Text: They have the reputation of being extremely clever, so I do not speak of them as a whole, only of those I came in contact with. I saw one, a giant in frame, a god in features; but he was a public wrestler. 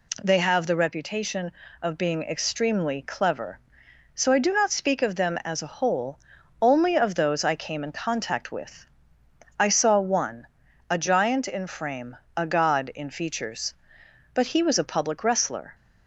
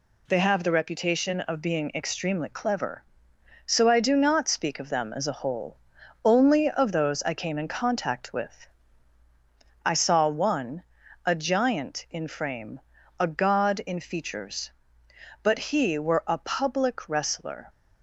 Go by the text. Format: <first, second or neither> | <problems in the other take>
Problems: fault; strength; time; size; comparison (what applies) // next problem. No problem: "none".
first | says "were" for "was"; at 15.9 s